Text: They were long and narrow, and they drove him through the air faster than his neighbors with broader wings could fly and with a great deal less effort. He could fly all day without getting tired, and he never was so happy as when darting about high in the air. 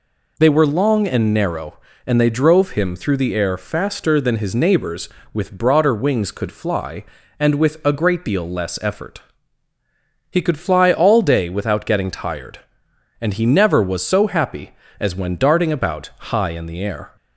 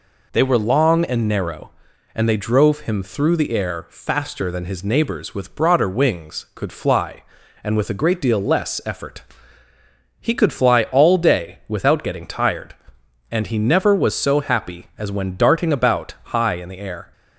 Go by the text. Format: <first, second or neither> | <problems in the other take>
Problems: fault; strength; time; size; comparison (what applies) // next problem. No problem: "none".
neither | none